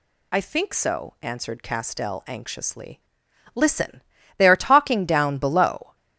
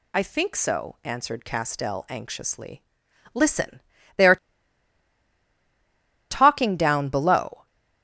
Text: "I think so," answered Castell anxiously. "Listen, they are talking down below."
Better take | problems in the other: first | pauses between "are" and "talking"; strong; at 4.3 s; 1.9 s long

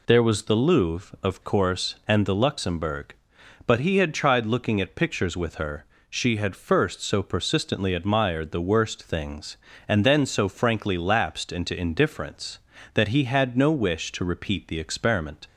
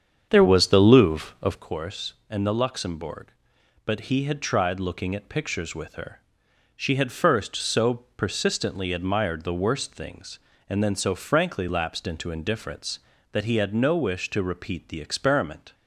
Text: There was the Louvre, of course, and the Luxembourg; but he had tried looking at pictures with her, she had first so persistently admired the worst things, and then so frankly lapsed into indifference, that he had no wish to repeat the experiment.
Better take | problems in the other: first | starts louder than the rest; strong; until 1.7 s; 7.5 dB

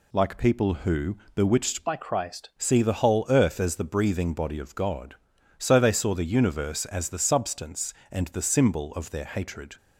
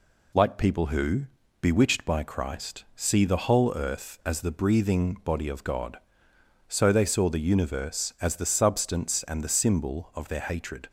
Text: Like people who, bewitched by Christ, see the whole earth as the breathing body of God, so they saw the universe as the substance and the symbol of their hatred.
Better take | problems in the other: second | changes voice from "by" to "Christ"; from 1.8 to 2.4 s; 0.6 s long

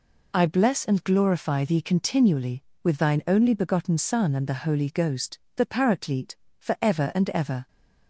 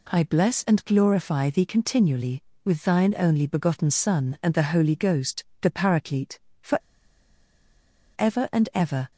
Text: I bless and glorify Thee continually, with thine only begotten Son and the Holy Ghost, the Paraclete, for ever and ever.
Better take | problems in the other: first | pauses between "for" and "ever"; strong; at 6.7 s; 1.3 s long

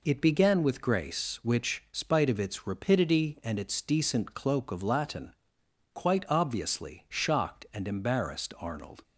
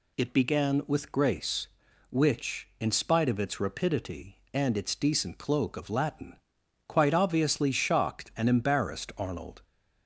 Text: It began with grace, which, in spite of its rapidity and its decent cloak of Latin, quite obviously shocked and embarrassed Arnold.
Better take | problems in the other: second | skips "in"; at 1.8 s

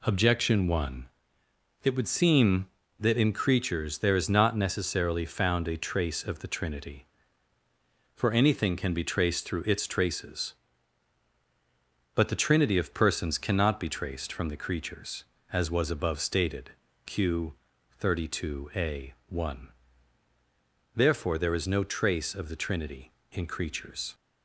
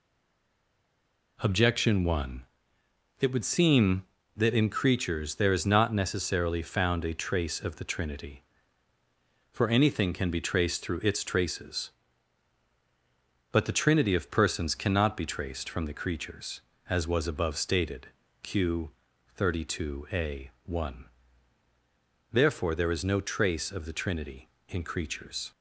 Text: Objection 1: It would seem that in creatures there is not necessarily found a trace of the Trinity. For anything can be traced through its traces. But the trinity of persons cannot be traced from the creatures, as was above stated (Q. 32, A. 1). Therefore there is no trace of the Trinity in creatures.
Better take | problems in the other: first | stays silent before the first word; noticeable; until 1.3 s; 1.3 s long

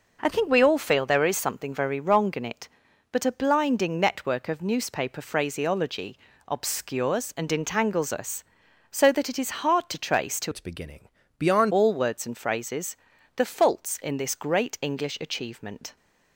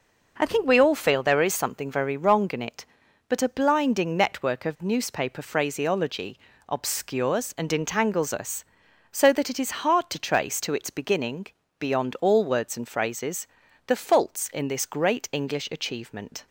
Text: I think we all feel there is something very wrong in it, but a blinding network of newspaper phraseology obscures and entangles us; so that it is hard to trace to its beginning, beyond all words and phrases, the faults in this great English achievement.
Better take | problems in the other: second | pauses between "phraseology" and "obscures"; slight; at 6.1 s; 0.28 s long; slight in the second // changes voice from "its" to "beyond"; from 10.5 to 11.7 s; 1.2 s long

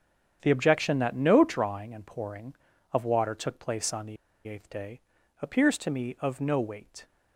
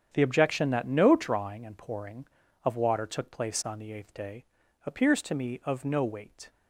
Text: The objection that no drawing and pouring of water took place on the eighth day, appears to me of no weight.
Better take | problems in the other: second | starts louder than the rest; strong; until 1.4 s; 8 dB; strong in the second // pauses between "the" and "eighth"; slight; at 4.1 s; 0.31 s long

